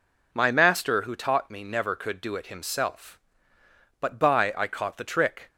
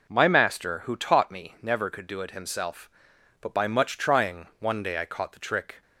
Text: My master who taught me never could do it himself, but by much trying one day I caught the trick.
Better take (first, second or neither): second